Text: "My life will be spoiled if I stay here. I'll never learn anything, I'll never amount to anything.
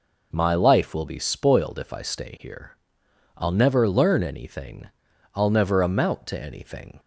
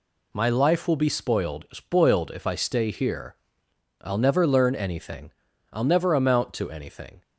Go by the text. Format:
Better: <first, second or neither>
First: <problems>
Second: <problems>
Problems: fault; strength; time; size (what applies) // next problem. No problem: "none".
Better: first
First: none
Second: says "spoiled" twice; at 1.7 s